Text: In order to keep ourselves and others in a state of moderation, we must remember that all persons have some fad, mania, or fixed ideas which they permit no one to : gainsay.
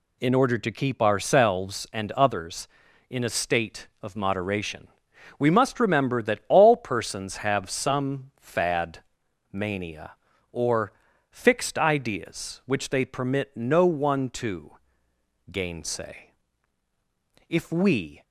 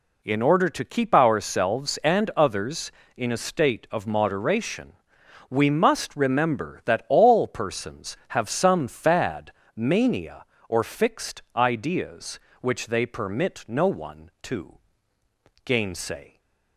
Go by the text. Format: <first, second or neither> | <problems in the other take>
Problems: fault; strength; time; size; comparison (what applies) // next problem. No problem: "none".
second | pauses between "or" and "fixed"; at 10.9 s; 0.40 s long // goes on to say "If we"; noticeable; from 17.4 s on; 0.74 s long